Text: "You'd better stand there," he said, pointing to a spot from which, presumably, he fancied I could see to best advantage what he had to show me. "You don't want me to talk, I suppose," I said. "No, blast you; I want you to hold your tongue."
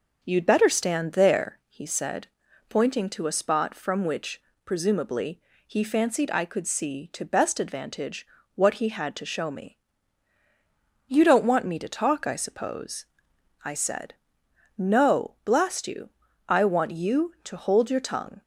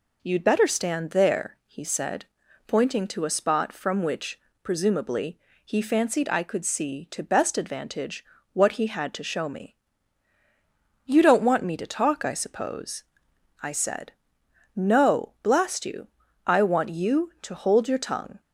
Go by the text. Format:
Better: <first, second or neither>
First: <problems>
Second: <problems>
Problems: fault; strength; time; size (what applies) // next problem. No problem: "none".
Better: second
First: starts louder than the rest; noticeable; until 1.6 s; 6 dB // pauses between "advantage" and "what"; slight; at 8.2 s; 0.28 s long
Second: pauses between "advantage" and "what"; slight; at 8.2 s; 0.28 s long